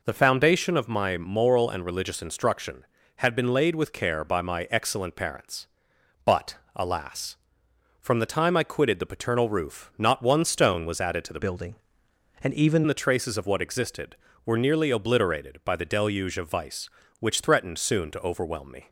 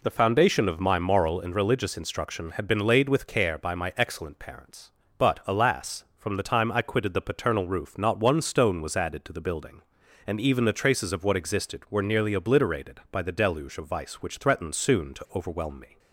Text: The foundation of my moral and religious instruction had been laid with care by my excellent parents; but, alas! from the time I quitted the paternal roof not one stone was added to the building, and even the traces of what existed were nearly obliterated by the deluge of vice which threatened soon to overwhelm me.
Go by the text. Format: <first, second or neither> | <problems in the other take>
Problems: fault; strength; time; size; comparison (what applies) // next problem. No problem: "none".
second | changes voice from "building" to "even"; from 11.4 to 12.8 s; 1.4 s long